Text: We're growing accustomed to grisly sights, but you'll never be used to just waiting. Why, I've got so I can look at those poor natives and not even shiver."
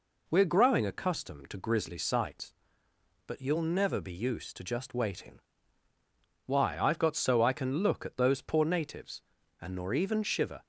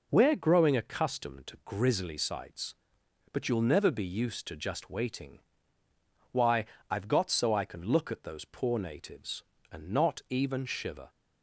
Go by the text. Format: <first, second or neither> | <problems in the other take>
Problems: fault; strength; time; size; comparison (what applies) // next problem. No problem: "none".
second | says "nor" for "not"; at 9.7 s